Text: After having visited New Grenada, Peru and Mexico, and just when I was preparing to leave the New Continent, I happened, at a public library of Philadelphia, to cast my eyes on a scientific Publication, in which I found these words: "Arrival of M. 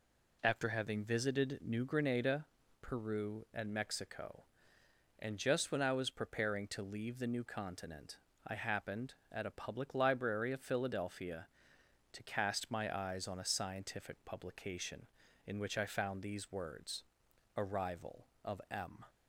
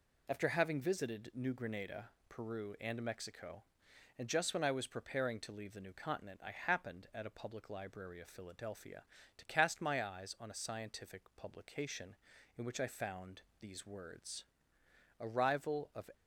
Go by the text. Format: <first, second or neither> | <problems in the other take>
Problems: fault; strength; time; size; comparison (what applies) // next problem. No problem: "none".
first | pauses between "found" and "these"; slight; at 13.4 s; 0.18 s long // stops before "M"; at 16.1 s